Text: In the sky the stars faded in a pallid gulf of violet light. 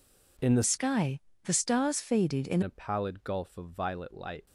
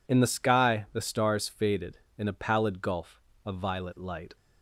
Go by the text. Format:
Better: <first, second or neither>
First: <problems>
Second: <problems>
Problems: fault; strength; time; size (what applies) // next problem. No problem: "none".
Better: second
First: changes voice from "sky" to "in"; from 0.6 to 2.6 s; 2.0 s long // pauses between "sky" and "the"; slight; at 1.1 s; 0.24 s long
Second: none